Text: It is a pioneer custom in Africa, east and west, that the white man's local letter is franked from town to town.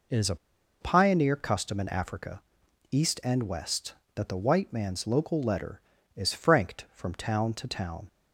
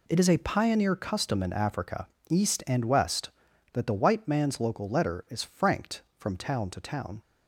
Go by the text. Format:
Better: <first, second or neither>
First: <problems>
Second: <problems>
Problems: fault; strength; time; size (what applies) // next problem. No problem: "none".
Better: second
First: pauses between "a" and "pioneer"; at 0.3 s; 0.45 s long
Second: none